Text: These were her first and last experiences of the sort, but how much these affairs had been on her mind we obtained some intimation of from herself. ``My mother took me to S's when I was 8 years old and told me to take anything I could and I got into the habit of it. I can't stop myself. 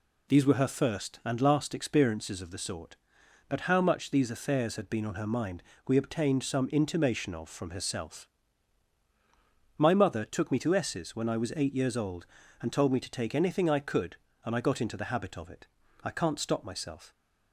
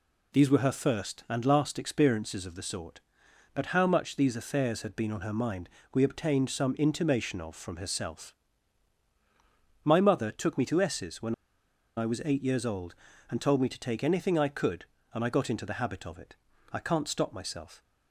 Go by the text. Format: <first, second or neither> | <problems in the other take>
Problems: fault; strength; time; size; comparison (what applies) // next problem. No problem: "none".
first | pauses between "mind" and "we"; slight; at 5.6 s; 0.26 s long; slight in the first // pauses between "when" and "I"; noticeable; at 11.3 s; 0.62 s long